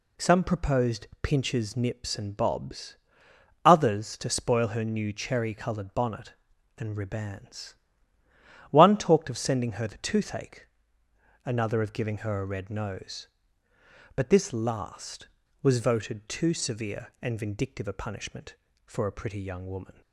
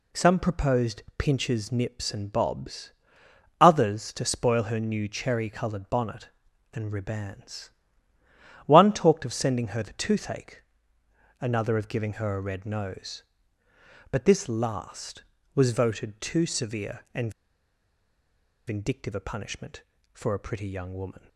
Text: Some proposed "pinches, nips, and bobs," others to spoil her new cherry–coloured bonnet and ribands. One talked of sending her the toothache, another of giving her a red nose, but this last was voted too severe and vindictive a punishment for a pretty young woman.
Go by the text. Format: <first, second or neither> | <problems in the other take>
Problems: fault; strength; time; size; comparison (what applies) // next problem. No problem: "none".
first | pauses between "and" and "vindictive"; strong; at 17.3 s; 1.3 s long